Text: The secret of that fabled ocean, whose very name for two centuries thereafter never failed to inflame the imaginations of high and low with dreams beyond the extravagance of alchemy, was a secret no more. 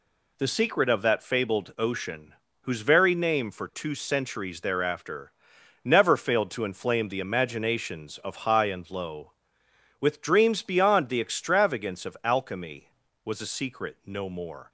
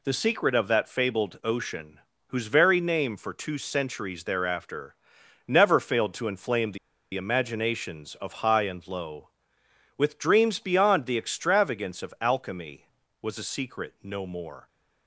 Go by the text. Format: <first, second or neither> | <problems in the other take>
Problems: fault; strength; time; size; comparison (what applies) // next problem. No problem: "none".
first | pauses between "thereafter" and "never"; noticeable; at 4.9 s; 0.52 s long; noticeable in the first // pauses between "the" and "imaginations"; at 6.7 s; 0.36 s long